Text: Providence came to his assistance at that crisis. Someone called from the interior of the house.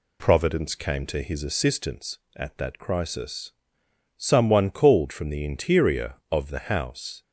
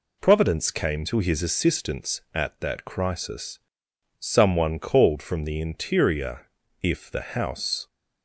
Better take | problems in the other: first | says "if" for "of"; at 6.8 s

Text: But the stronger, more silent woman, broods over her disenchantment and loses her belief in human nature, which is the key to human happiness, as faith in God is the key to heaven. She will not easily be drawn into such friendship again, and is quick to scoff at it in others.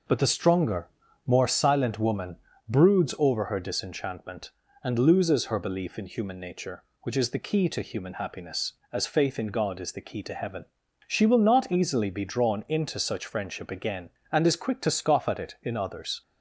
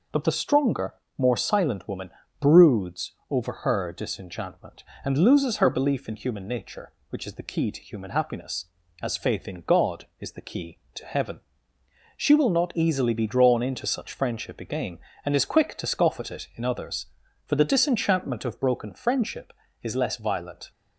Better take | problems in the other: first | pauses between "broods" and "over"; slight; at 3.1 s; 0.16 s long // goes on to say "For the disenchantment of broken friendship is less violent"; strong; from 17.4 s on; 3.2 s long

